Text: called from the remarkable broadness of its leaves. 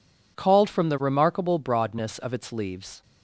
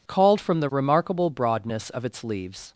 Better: neither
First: none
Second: none

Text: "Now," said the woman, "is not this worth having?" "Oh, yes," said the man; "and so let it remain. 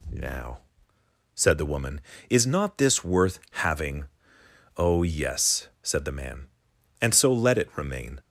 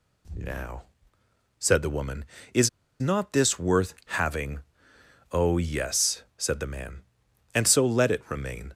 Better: first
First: none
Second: pauses between "is" and "not"; slight; at 2.6 s; 0.32 s long

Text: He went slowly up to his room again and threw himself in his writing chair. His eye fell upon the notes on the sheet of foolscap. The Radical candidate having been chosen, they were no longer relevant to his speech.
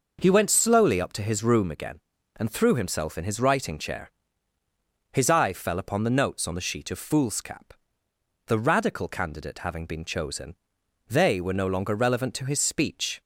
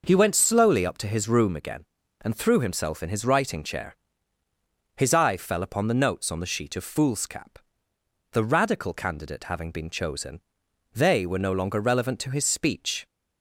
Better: neither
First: none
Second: none

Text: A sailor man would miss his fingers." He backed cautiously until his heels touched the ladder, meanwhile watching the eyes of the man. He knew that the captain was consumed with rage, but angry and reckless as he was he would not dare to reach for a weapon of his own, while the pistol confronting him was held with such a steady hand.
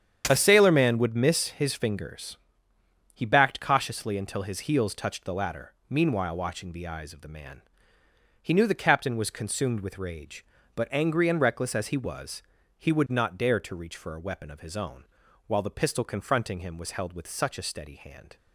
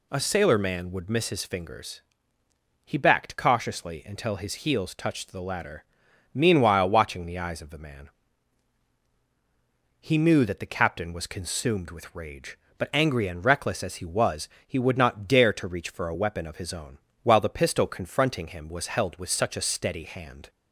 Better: second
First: starts louder than the rest; strong; until 1.2 s; 8.5 dB // skips "that"; at 8.6 s // pauses between "was" and "he"; slight; at 12.4 s; 0.34 s long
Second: pauses between "was" and "he"; slight; at 14.4 s; 0.20 s long

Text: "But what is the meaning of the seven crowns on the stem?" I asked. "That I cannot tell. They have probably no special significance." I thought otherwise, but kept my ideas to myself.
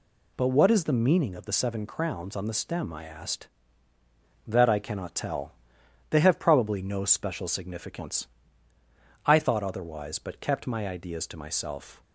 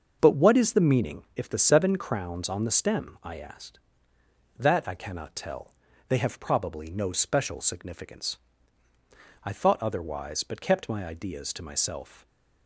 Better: first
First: none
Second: starts louder than the rest; until 1.2 s; 6.5 dB // says "if" for "of"; at 1.3 s // stays silent after the last word; slight; from 12.1 s on; 0.5 s long

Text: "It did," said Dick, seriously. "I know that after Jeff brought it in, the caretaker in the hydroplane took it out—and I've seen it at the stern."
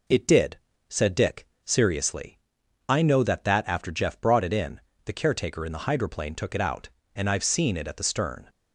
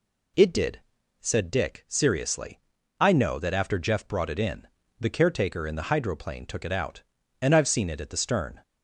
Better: second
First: says "that" twice; at 3.4 s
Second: none

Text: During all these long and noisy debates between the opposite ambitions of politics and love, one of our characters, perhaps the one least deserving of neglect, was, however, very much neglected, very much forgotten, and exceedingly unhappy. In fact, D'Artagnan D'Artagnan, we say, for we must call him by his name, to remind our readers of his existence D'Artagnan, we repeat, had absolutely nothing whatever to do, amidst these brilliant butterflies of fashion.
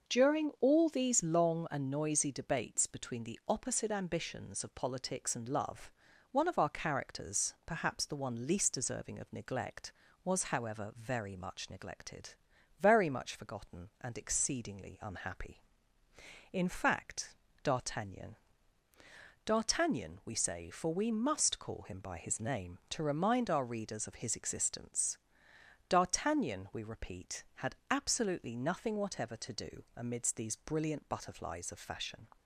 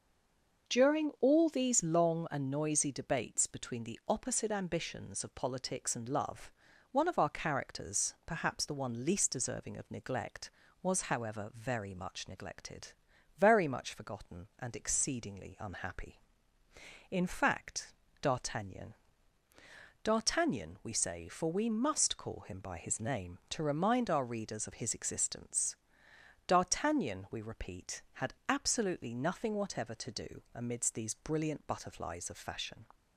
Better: first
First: pauses between "D'Artagnan" and "D'Artagnan"; at 18.3 s; 1.0 s long // pauses between "existence" and "D'Artagnan"; noticeable; at 25.1 s; 0.74 s long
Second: stays silent before the first word; slight; until 0.6 s; 0.6 s long // pauses between "D'Artagnan" and "D'Artagnan"; at 18.9 s; 1.0 s long // pauses between "existence" and "D'Artagnan"; noticeable; at 25.7 s; 0.74 s long

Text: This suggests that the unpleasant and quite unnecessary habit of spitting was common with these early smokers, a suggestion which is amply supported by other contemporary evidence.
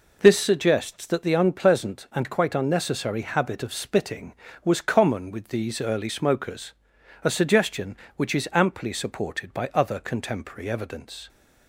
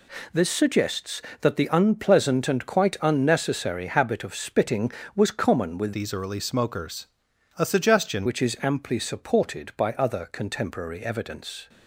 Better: first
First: none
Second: changes voice from "these" to "suggestion"; from 5.9 to 8.2 s; 2.3 s long

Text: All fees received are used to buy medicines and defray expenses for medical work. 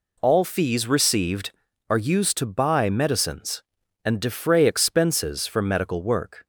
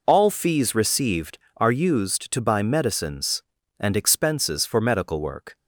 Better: first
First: none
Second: skips "defray"; at 3.9 s

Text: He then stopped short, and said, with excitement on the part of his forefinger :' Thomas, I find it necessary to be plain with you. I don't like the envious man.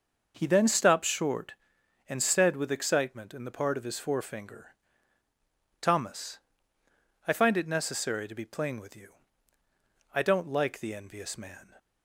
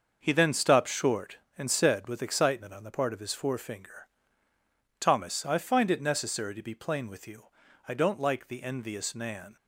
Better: second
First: starts louder than the rest; until 1.3 s; 6 dB // says "in" for "on"; at 3.3 s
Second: starts louder than the rest; until 1.2 s; 6.5 dB

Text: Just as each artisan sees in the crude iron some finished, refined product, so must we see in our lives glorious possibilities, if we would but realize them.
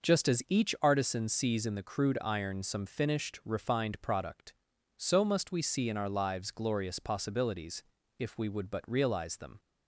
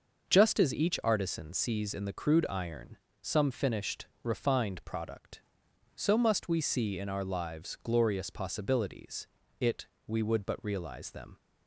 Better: first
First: none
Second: pauses between "iron" and "some"; slight; at 2.9 s; 0.24 s long // says "it" for "if"; at 9.6 s

